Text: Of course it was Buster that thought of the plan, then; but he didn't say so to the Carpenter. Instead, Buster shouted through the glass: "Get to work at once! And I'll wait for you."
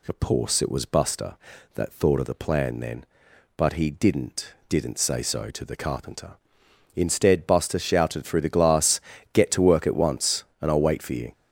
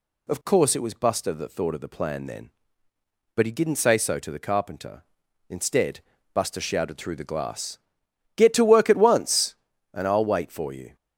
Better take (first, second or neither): second